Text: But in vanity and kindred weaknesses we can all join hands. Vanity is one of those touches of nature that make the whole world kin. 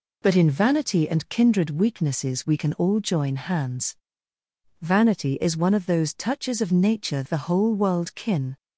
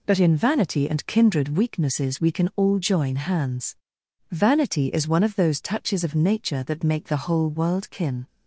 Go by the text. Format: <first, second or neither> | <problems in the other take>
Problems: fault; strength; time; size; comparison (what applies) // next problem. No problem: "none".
second | skips "that make"; at 7.2 s